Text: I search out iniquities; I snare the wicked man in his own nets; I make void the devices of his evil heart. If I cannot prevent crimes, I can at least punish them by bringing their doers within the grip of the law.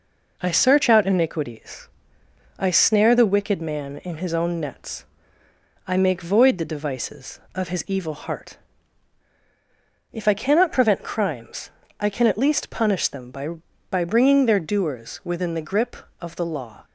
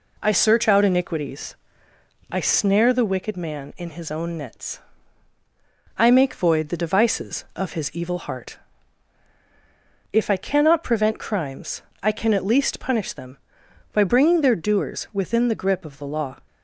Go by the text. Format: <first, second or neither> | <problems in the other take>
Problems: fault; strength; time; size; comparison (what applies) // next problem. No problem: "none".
second | says "by" twice; at 13.8 s